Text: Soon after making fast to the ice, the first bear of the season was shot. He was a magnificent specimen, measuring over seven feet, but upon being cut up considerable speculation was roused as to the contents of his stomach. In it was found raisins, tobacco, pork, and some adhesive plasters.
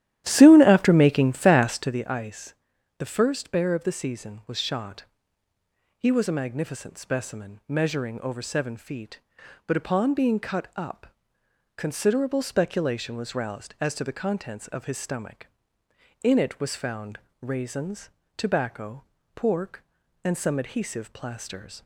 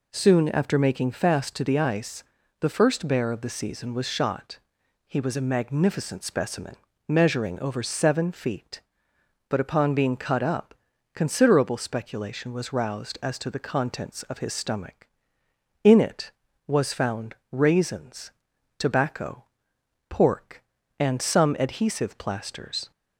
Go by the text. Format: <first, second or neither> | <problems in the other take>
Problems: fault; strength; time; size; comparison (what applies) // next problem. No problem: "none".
second | starts louder than the rest; strong; until 2.0 s; 12.5 dB // pauses between "up" and "considerable"; noticeable; at 11.0 s; 0.70 s long; also in the second // pauses between "found" and "raisins"; slight; at 17.1 s; 0.22 s long; slight in the second